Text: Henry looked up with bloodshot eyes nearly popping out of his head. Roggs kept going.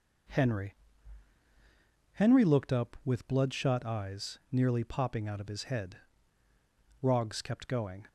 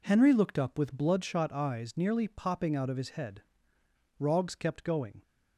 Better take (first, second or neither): second